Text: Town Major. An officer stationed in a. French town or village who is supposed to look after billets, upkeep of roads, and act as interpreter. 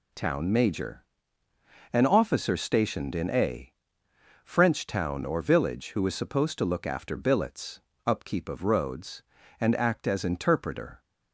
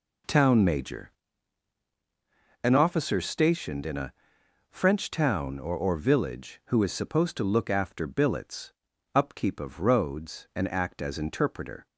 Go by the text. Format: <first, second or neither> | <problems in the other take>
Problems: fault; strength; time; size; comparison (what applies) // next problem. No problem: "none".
first | says "or" twice; at 5.7 s